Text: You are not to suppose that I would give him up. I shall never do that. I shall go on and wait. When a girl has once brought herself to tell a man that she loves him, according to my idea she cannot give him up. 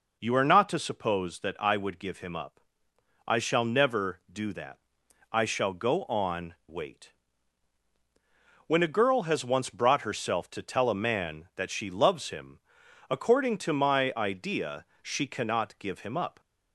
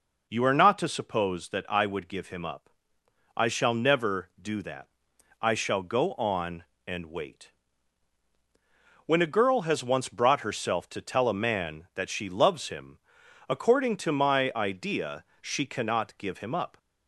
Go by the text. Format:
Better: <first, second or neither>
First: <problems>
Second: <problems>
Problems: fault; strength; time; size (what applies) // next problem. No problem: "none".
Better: second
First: skips "and"; at 6.6 s // pauses between "idea" and "she"; slight; at 14.8 s; 0.18 s long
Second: pauses between "idea" and "she"; slight; at 15.2 s; 0.18 s long